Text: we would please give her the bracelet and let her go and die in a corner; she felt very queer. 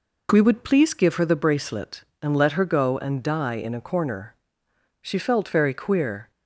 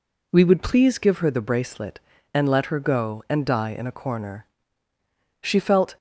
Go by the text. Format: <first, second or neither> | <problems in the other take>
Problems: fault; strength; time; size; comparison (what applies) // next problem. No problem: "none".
first | stops before "very queer"; at 5.9 s